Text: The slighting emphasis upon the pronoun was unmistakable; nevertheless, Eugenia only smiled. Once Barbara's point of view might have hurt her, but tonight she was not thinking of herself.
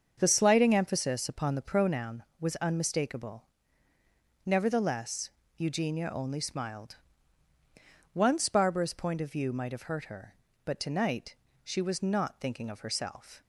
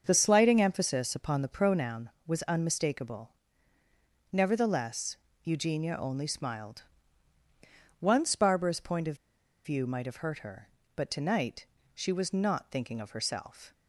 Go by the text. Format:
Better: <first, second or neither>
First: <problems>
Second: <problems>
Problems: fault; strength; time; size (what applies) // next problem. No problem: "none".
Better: first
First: starts louder than the rest; until 1.1 s; 6.5 dB // pauses between "tonight" and "she"; slight; at 11.3 s; 0.30 s long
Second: starts louder than the rest; until 1.0 s; 7 dB // pauses between "of" and "view"; noticeable; at 9.1 s; 0.47 s long // pauses between "tonight" and "she"; slight; at 11.6 s; 0.30 s long